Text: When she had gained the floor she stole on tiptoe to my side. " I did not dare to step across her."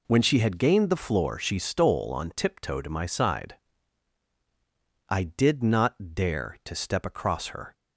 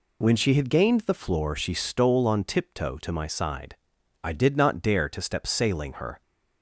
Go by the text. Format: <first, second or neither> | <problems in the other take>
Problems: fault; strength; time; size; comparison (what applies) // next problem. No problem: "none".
first | says "sailing" for "across"; at 5.4 s